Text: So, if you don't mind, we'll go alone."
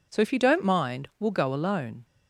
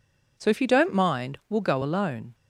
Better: neither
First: none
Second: none

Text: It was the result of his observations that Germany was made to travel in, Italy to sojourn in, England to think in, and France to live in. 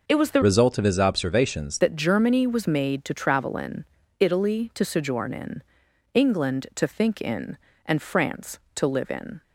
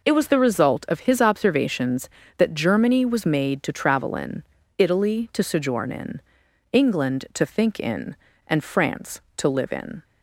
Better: second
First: changes voice from "result" to "observations"; from 0.4 to 1.7 s; 1.3 s long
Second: none

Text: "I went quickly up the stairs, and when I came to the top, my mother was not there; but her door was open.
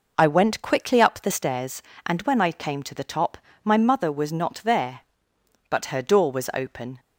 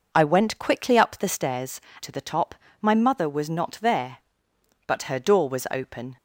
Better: first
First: none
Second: skips "and when I came"; at 1.9 s

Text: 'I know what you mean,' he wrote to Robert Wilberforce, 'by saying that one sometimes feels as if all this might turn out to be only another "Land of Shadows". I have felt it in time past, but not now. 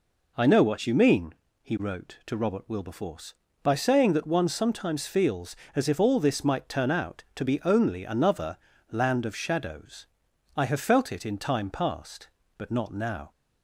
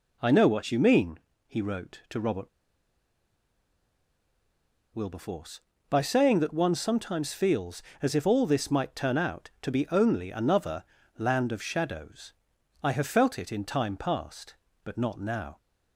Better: first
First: pauses between "another" and "Land"; slight; at 8.5 s; 0.34 s long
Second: pauses between "Robert" and "Wilberforce"; strong; at 2.4 s; 2.4 s long // pauses between "another" and "Land"; slight; at 10.8 s; 0.34 s long

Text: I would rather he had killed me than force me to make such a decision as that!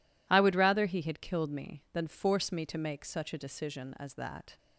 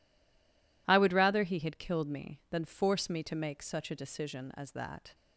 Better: first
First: none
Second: stays silent before the first word; slight; until 0.8 s; 0.8 s long

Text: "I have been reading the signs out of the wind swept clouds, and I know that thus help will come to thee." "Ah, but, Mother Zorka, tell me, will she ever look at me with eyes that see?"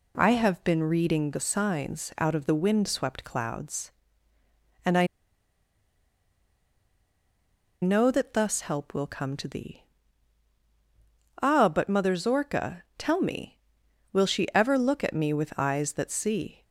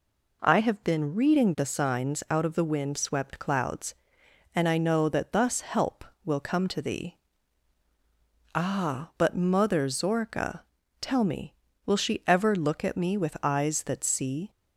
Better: second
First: pauses between "I" and "know"; strong; at 5.0 s; 2.7 s long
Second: none

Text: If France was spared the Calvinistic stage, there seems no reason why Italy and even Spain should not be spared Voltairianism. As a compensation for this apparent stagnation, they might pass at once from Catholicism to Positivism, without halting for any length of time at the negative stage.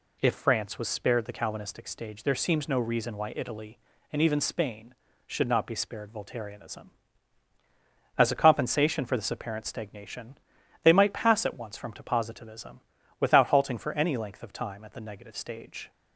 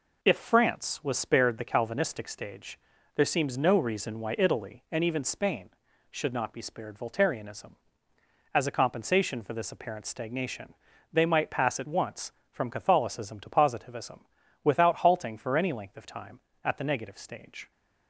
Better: second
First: skips "Catholicism"; at 11.9 s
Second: none

